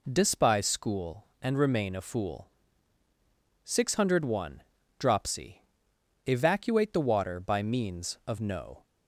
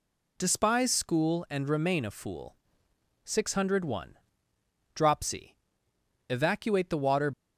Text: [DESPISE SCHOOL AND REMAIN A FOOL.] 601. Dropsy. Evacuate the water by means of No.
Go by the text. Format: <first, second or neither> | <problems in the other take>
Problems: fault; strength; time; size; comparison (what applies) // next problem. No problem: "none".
first | stops before "by means of No"; at 7.3 s